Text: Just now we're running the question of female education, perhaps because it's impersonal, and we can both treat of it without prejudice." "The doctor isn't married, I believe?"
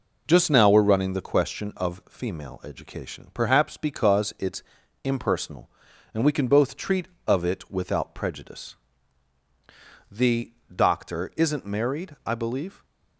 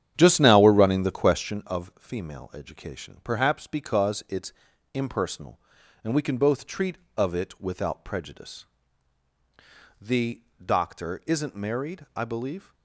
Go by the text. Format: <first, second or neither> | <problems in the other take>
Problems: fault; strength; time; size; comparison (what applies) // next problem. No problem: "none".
first | starts louder than the rest; strong; until 1.7 s; 9.5 dB // pauses between "it's" and "impersonal"; at 4.5 s; 0.40 s long; also in the first // pauses between "The" and "doctor"; slight; at 10.4 s; 0.20 s long; slight in the first